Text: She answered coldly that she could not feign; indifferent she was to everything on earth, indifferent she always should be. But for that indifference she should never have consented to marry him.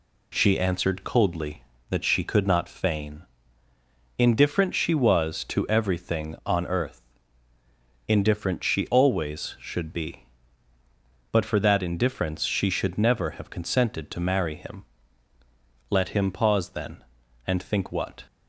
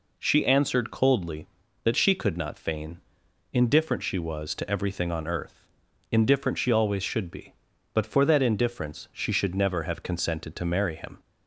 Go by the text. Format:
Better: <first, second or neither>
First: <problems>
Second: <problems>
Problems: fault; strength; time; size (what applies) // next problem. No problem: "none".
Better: second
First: goes on to say "Let him pause then and think what"; strong; from 15.9 s on; 2.3 s long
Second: none